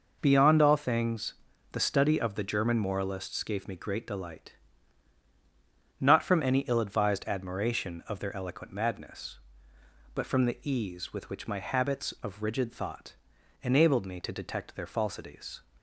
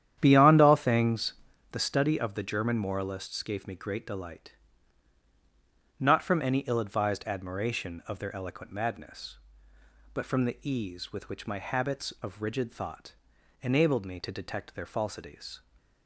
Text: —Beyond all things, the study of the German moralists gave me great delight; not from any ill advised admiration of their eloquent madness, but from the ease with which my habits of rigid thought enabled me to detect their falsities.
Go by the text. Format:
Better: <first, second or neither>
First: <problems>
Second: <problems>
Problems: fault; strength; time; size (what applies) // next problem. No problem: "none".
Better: first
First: pauses between "thought" and "enabled"; noticeable; at 13.1 s; 0.48 s long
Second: starts louder than the rest; strong; until 1.7 s; 10 dB // pauses between "thought" and "enabled"; noticeable; at 13.1 s; 0.48 s long